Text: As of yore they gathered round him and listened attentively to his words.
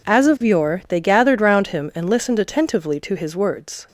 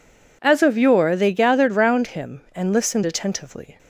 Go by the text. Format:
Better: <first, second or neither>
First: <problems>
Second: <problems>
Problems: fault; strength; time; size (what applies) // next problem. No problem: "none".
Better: first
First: none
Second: stops before "to his words"; at 3.7 s